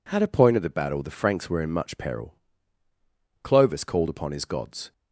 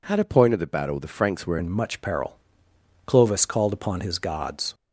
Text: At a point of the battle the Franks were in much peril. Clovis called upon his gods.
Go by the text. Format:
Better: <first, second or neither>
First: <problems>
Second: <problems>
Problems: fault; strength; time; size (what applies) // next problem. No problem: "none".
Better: first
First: none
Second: changes voice at "in"; from 1.5 s on; 3.2 s long